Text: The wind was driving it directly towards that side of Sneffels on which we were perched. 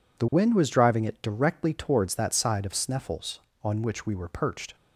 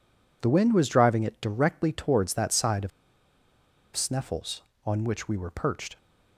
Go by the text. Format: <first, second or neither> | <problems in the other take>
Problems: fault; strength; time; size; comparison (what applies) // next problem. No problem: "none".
first | pauses between "of" and "Sneffels"; at 2.9 s; 1.0 s long